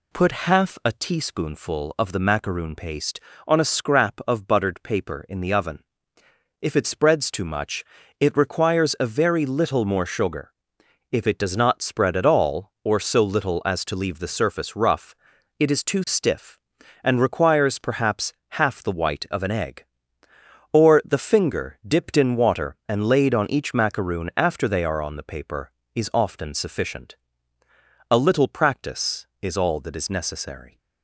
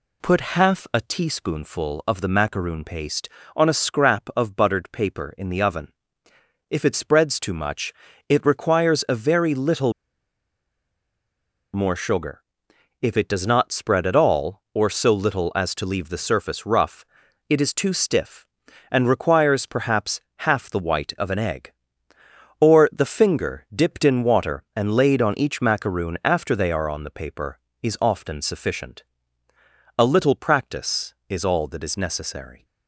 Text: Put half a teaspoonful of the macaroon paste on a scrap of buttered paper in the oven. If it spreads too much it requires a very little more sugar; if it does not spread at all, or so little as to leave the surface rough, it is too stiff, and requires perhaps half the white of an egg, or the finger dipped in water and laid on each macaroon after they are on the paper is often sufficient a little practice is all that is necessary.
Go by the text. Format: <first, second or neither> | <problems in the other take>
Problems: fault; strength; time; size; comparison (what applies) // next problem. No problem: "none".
first | pauses between "much" and "it"; at 7.9 s; 0.38 s long; also in the first // pauses between "little" and "more"; strong; at 9.9 s; 1.8 s long // pauses between "perhaps" and "half"; slight; at 20.1 s; 0.20 s long; slight in the first // pauses between "sufficient" and "a"; noticeable; at 29.0 s; 0.94 s long; noticeable in the first